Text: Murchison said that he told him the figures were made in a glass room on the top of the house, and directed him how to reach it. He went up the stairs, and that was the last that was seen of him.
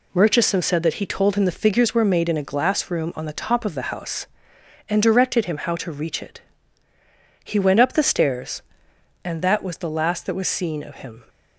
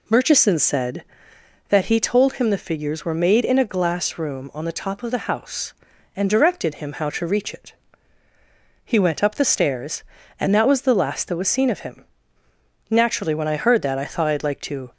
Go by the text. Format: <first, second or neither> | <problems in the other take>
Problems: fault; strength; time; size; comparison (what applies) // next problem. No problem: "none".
first | goes on to say "Naturally when I heard that I thought I'd like to"; strong; from 12.8 s on; 2.0 s long